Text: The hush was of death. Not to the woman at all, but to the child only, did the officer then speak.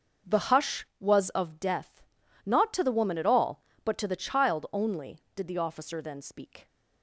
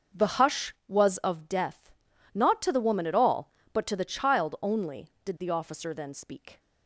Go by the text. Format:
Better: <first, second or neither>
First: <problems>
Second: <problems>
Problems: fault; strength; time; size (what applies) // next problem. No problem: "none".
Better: neither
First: starts louder than the rest; until 1.4 s; 6.5 dB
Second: starts louder than the rest; until 1.3 s; 6.5 dB